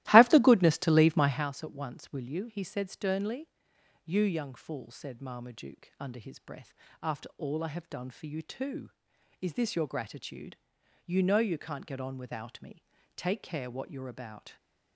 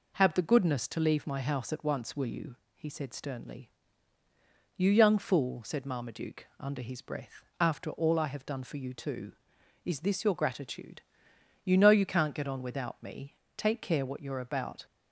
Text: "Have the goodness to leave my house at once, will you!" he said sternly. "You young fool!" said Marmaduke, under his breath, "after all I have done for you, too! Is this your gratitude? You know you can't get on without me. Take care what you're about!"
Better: second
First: starts louder than the rest; strong; until 1.5 s; 16.5 dB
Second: none

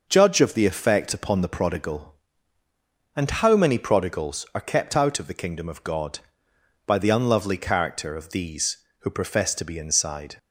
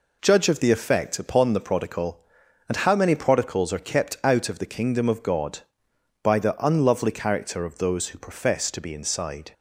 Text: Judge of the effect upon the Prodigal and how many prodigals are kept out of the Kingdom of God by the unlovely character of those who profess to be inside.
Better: second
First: says "these" for "those"; at 8.2 s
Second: none

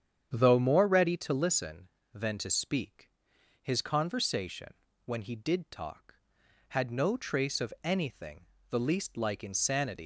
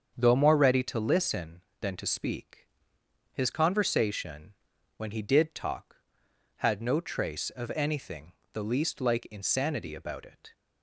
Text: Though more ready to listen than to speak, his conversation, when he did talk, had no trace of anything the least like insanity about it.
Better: second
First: starts louder than the rest; strong; until 1.4 s; 8.5 dB // pauses between "anything" and "the"; slight; at 8.4 s; 0.24 s long // stops before "about it"; at 10.0 s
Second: starts louder than the rest; until 1.1 s; 7 dB // pauses between "anything" and "the"; slight; at 8.3 s; 0.22 s long

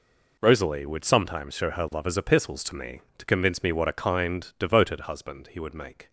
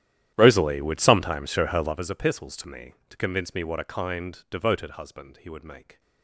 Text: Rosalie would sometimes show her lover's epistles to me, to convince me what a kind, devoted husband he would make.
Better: first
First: none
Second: starts louder than the rest; strong; until 2.0 s; 12 dB

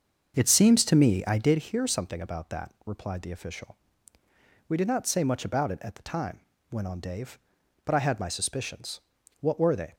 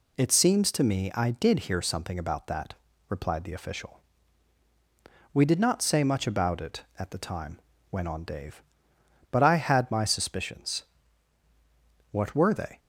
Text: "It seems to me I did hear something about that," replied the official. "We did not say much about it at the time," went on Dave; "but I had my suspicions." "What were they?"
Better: second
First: starts louder than the rest; until 1.7 s; 6.5 dB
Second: none

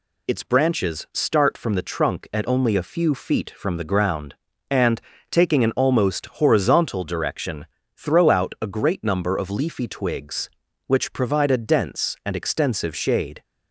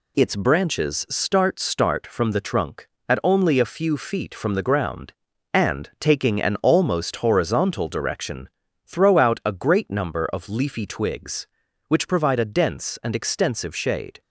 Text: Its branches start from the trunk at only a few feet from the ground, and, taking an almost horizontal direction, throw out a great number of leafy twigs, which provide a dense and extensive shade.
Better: first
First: none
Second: says "start" twice; at 1.5 s

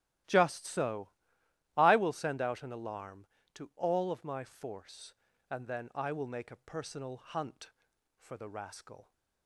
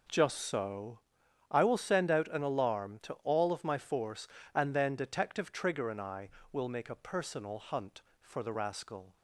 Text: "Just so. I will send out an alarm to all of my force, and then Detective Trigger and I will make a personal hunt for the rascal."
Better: second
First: starts louder than the rest; strong; until 1.9 s; 15 dB // skips "Detective Trigger and"; at 5.9 s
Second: none

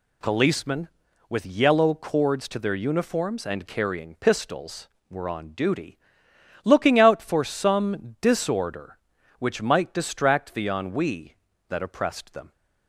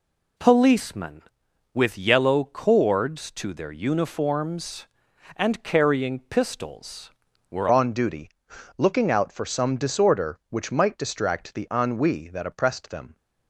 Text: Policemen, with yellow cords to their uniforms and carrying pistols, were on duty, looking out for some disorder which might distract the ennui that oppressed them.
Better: first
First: none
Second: changes voice at "on"; from 7.7 s on; 5.4 s long

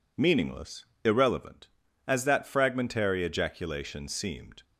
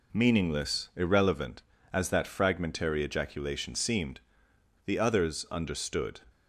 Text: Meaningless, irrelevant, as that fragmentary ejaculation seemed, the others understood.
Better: second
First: stops before "the others understood"; at 4.6 s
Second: none

